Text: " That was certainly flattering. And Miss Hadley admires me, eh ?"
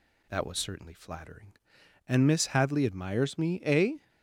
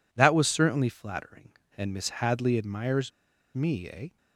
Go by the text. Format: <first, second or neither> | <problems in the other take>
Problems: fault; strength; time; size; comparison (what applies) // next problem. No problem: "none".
first | pauses between "admires" and "me"; noticeable; at 3.1 s; 0.46 s long